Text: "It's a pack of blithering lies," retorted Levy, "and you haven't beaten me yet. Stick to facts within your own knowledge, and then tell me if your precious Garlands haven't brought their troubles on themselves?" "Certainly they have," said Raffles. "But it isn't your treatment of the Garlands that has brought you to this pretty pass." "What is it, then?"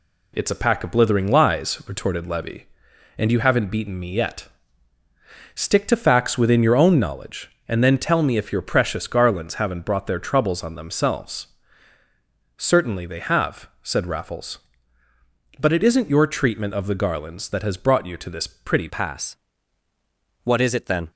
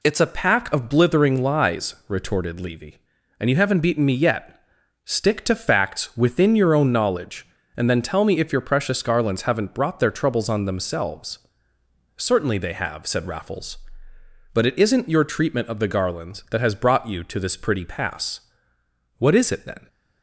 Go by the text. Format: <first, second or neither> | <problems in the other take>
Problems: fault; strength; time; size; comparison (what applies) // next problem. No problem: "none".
second | changes voice at "pass"; from 18.8 s on; 2.3 s long